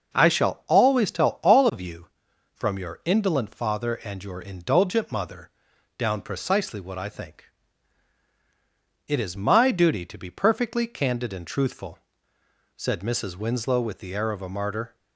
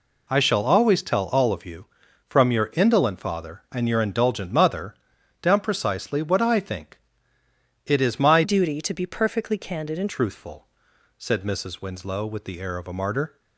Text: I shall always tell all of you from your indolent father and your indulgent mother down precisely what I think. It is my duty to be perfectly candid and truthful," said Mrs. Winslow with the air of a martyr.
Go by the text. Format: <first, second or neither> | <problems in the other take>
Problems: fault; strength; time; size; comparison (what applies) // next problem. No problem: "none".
first | pauses between "mother" and "down"; noticeable; at 4.9 s; 0.48 s long; noticeable in the first // changes voice from "duty" to "and"; from 8.4 to 10.0 s; 1.6 s long